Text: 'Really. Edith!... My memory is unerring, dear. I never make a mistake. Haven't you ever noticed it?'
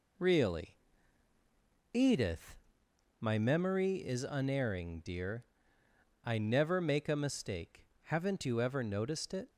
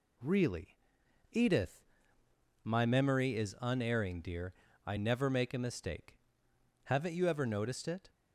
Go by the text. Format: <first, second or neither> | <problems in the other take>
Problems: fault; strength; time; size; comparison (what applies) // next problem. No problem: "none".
second | gets quieter; noticeable; throughout; 4.5 dB